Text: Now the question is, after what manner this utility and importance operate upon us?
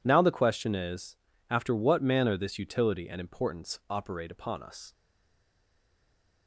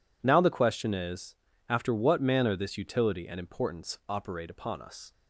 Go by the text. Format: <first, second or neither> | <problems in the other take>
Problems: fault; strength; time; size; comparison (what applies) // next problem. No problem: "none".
second | stays silent after the last word; noticeable; from 4.9 s on; 1.5 s long